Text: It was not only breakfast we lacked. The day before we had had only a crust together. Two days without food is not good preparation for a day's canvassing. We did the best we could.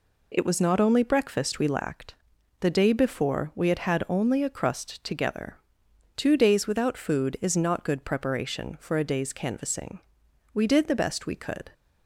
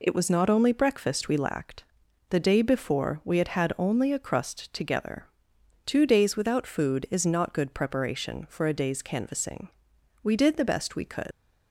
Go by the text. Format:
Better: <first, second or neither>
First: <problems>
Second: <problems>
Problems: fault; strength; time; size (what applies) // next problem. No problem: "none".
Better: first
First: none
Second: leaves "could" unfinished; at 11.3 s; 110 ms